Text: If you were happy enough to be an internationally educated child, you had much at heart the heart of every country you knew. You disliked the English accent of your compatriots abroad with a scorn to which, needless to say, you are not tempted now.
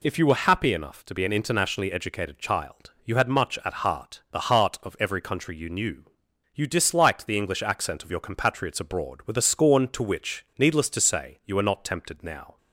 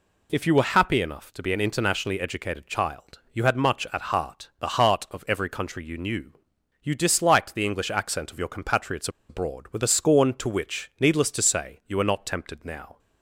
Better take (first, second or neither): first